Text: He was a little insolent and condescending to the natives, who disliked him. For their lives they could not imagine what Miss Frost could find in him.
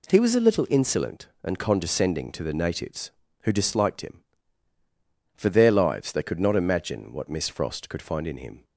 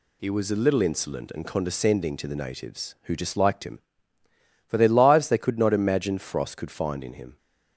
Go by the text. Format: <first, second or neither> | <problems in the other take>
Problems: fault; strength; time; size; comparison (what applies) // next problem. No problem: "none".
first | skips "what Miss"; at 6.1 s